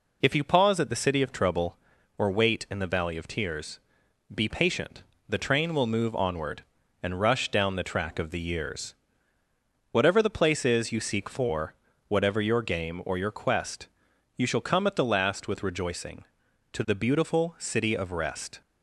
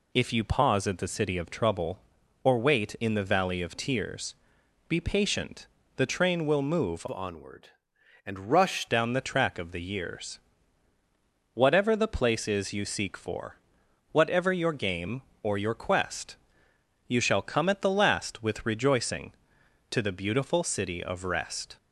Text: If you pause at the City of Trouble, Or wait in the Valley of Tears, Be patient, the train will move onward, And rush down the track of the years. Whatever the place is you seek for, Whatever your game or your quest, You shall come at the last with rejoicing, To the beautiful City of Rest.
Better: first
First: none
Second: changes voice from "onward" to "rush"; from 7.1 to 8.8 s; 1.7 s long

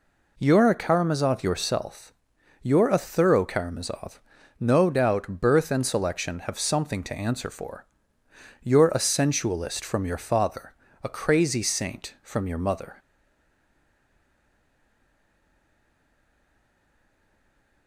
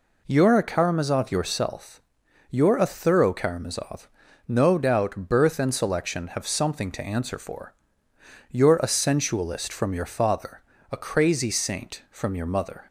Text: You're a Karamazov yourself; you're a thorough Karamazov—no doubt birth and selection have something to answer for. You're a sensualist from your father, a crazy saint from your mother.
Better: second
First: stays silent after the last word; strong; from 12.9 s on; 4.9 s long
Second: none

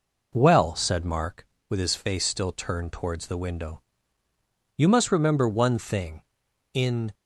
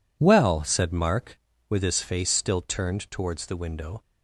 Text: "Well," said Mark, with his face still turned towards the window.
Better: second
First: goes on to say "You must remember one thing in"; strong; from 4.7 s on; 2.3 s long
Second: none

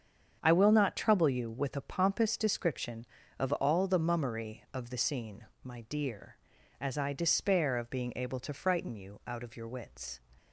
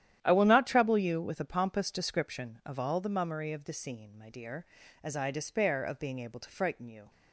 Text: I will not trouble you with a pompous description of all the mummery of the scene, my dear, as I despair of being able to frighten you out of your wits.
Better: first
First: starts louder than the rest; strong; until 1.4 s; 7.5 dB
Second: starts louder than the rest; strong; until 1.2 s; 11 dB // stops before "out of your wits"; at 7.0 s

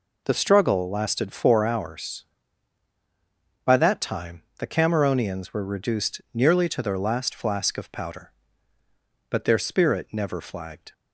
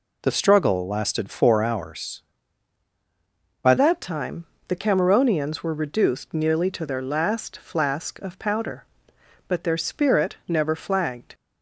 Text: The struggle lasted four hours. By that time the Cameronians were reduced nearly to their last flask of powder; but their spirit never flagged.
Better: first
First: pauses between "time" and "the"; slight; at 4.4 s; 0.15 s long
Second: changes voice at "that"; from 3.7 s on; 7.6 s long // pauses between "time" and "the"; slight; at 4.4 s; 0.24 s long

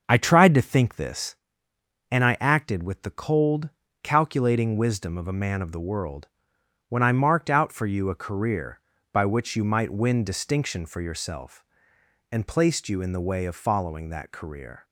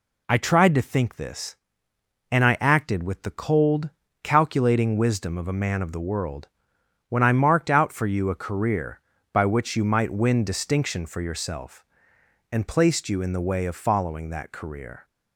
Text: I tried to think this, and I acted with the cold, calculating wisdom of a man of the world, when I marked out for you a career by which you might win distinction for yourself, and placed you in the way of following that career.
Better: second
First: starts louder than the rest; until 1.4 s; 6.5 dB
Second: none

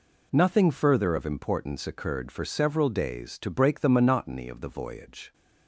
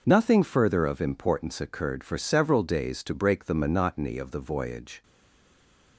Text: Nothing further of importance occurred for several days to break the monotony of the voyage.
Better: first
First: none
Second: stays silent after the last word; from 5.0 s on; 0.9 s long

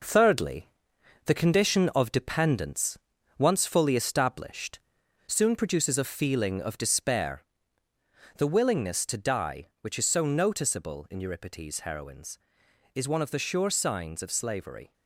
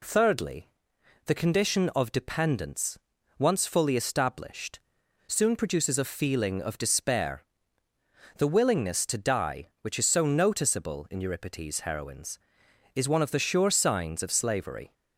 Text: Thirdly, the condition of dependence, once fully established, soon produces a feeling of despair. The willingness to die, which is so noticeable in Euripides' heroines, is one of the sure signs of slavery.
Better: second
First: gets quieter; throughout; 6.5 dB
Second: none

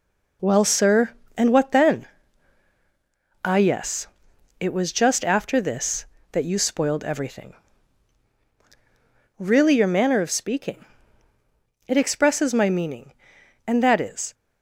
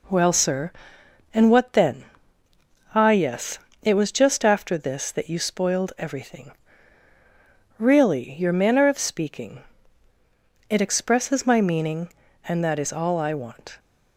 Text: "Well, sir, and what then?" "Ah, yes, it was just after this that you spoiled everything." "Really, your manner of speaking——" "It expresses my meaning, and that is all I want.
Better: second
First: stops before "all I want"; at 14.3 s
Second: none

